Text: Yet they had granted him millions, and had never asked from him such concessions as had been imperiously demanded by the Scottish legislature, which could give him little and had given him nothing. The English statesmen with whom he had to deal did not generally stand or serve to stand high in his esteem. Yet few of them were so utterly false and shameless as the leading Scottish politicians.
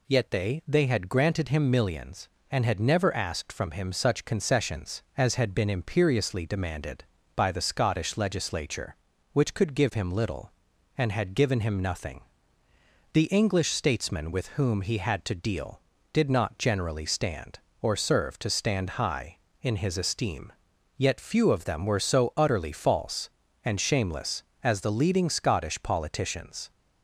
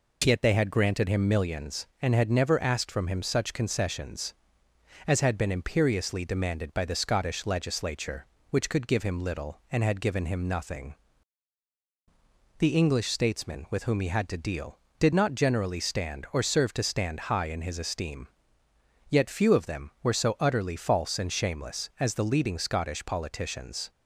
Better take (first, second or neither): second